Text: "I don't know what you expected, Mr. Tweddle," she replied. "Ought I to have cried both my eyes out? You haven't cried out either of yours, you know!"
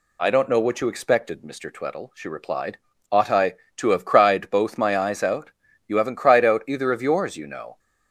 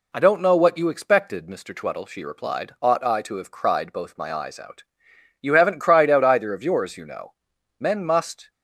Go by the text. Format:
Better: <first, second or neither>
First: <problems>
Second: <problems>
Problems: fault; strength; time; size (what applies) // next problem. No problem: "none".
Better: first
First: none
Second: goes on to say "Men must"; noticeable; from 7.8 s on; 0.70 s long